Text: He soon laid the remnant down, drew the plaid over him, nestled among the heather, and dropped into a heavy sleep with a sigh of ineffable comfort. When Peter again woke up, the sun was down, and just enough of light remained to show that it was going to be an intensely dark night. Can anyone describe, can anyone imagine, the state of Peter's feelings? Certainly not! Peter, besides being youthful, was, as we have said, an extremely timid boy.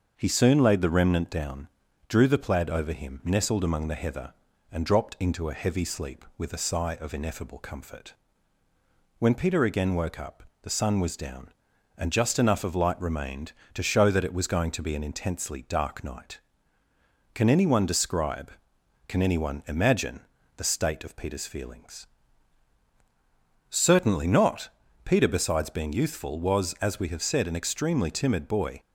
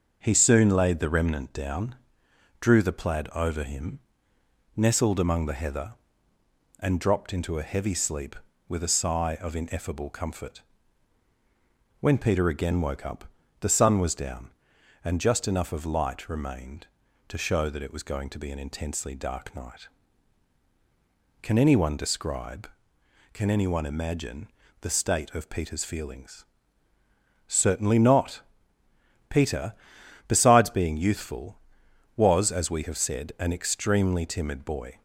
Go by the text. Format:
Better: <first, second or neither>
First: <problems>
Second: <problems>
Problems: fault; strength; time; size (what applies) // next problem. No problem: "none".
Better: neither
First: starts louder than the rest; until 1.1 s; 6.5 dB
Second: starts louder than the rest; until 1.2 s; 6.5 dB